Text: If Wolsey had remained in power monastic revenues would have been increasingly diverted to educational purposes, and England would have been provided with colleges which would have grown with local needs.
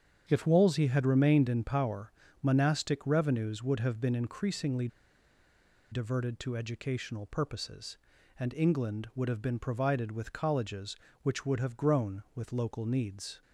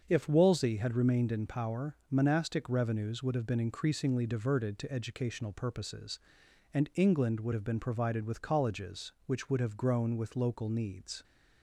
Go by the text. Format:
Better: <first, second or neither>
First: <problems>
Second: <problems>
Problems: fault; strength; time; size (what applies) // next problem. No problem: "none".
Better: second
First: starts louder than the rest; strong; until 1.2 s; 8 dB // pauses between "power" and "monastic"; slight; at 2.1 s; 0.30 s long // pauses between "increasingly" and "diverted"; at 4.8 s; 1.0 s long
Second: starts louder than the rest; until 1.1 s; 7 dB // pauses between "power" and "monastic"; slight; at 1.9 s; 0.16 s long